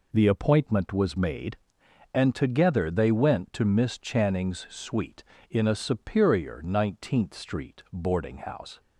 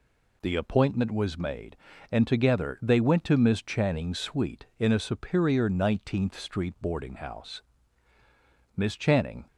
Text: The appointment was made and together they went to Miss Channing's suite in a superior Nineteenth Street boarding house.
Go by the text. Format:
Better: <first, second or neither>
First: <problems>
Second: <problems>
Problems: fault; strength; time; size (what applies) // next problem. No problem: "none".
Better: first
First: none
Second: goes on to say "Miss Channing"; noticeable; from 8.7 s on; 0.70 s long